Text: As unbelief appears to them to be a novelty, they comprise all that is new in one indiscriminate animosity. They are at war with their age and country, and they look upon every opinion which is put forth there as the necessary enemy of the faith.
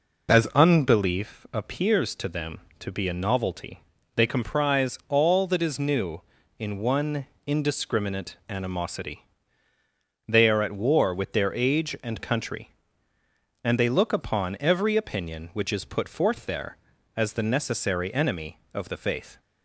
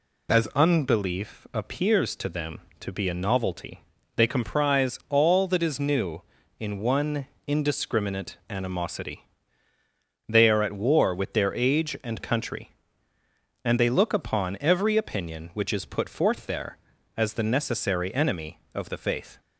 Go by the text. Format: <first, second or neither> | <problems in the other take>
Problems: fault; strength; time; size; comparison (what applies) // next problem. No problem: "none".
second | starts louder than the rest; noticeable; until 1.3 s; 4.5 dB // pauses between "one" and "indiscriminate"; slight; at 7.2 s; 0.22 s long; slight in the second